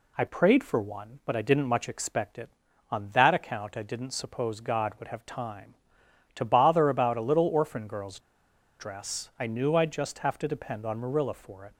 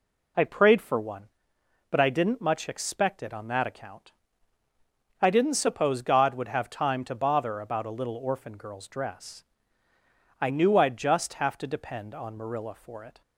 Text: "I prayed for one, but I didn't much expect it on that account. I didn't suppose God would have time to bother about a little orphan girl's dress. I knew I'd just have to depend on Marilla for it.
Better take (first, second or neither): second